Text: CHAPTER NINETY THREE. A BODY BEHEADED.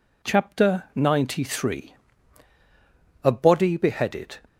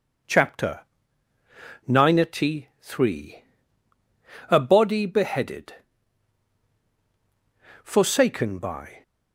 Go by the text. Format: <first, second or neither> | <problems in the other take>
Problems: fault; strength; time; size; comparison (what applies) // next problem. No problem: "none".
first | pauses between "CHAPTER" and "NINETY"; at 0.8 s; 1.0 s long // goes on to say "Forsaken by"; noticeable; from 7.8 s on; 1.1 s long